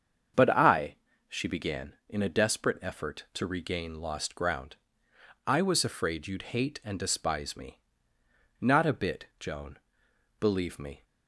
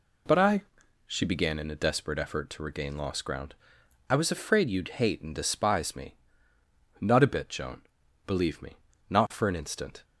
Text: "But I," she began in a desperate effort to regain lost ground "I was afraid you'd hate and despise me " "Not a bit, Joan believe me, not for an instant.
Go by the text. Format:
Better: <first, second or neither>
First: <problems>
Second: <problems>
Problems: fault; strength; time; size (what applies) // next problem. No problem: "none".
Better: second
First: starts louder than the rest; strong; until 1.6 s; 7.5 dB // pauses between "ground" and "I"; noticeable; at 4.7 s; 0.72 s long // pauses between "Joan" and "believe"; noticeable; at 9.7 s; 0.62 s long // stops before "not for an instant"; at 11.0 s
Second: pauses between "ground" and "I"; noticeable; at 3.5 s; 0.56 s long // pauses between "Joan" and "believe"; at 7.8 s; 0.44 s long